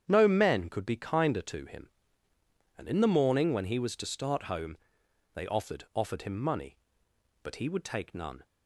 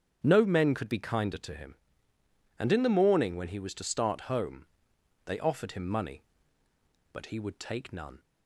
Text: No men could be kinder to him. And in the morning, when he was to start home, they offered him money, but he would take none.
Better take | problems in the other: second | starts louder than the rest; strong; until 1.0 s; 8.5 dB; strong in the second // says "offered" twice; at 5.9 s

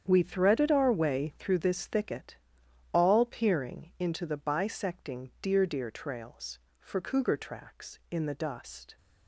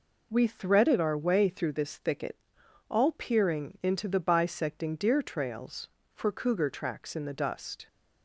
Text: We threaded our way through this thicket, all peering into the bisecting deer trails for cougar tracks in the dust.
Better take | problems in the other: second | starts louder than the rest; strong; until 1.0 s; 8.5 dB // says "deer" twice; at 5.6 s

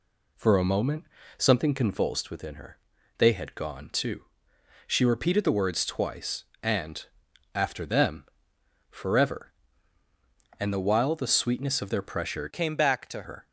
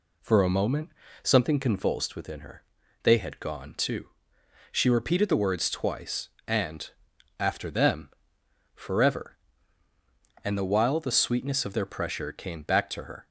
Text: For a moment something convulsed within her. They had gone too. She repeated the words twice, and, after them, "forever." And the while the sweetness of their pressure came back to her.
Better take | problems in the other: second | pauses between "moment" and "something"; slight; at 1.0 s; 0.34 s long; slight in the second // changes voice from "came" to "to"; from 12.5 to 13.2 s; 0.7 s long

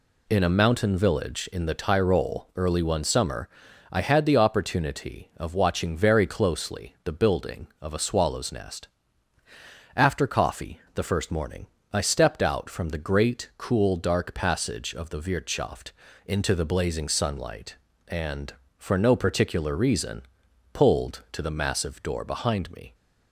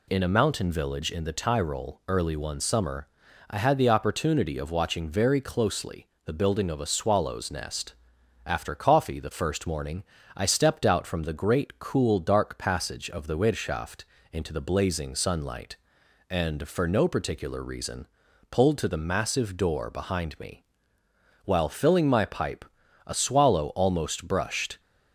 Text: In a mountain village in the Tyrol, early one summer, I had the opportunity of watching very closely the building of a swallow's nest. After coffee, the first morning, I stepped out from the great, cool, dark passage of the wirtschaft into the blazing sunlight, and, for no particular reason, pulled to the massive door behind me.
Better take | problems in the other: first | pauses between "closely" and "the"; slight; at 6.0 s; 0.18 s long // pauses between "wirtschaft" and "into"; slight; at 14.0 s; 0.28 s long; slight in the first // goes on to say "While filling my pipe a swallow almost brushed"; strong; from 21.4 s on; 3.3 s long

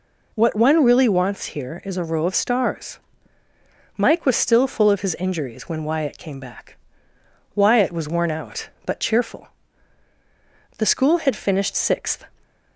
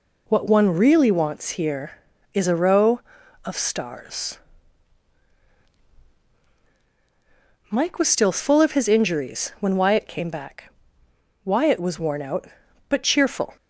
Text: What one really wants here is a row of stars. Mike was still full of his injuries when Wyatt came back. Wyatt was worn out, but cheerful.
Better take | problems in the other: second | goes on to say "The school had finished sixth"; from 10.7 s on; 1.5 s long

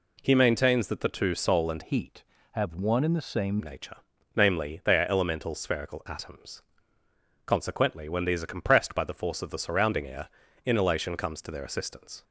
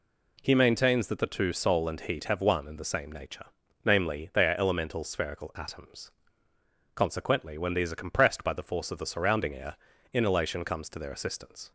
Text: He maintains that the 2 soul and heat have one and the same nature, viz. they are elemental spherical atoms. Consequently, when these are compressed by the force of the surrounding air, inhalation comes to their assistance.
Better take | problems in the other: second | changes voice from "heat" to "same"; from 1.8 to 3.6 s; 1.8 s long

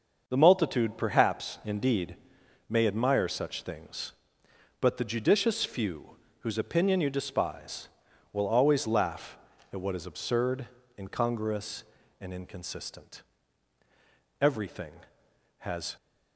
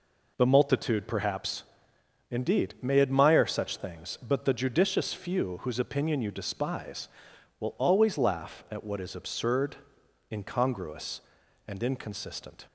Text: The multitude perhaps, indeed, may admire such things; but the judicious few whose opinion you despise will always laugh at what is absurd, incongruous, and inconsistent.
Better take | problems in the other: second | starts louder than the rest; until 1.2 s; 6.5 dB // pauses between "few" and "whose"; slight; at 6.1 s; 0.24 s long // goes on to say "Everything has"; from 14.4 s on; 1.5 s long

